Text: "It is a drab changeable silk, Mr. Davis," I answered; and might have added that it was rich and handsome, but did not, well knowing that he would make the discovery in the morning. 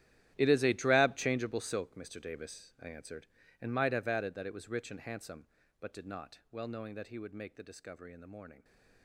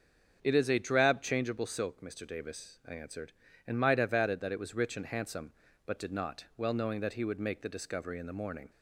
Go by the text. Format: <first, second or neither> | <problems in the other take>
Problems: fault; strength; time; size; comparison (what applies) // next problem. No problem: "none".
second | gets quieter; strong; throughout; 16 dB // starts louder than the rest; strong; until 1.3 s; 11.5 dB; also in the second